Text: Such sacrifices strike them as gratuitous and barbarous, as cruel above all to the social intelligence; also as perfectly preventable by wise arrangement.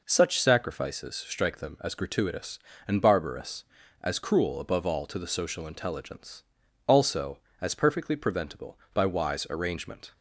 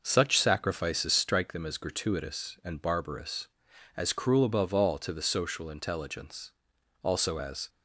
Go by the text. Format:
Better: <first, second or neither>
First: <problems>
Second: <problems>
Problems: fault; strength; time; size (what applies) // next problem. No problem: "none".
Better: first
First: none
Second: stops before "perfectly preventable by wise arrangement"; at 7.6 s